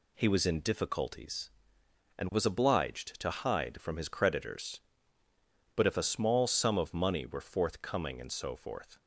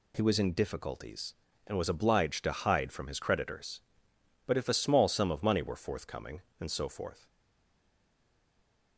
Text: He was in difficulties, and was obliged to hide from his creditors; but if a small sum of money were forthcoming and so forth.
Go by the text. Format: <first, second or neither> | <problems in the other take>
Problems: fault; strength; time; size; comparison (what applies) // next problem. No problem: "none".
first | stays silent after the last word; noticeable; from 7.2 s on; 1.7 s long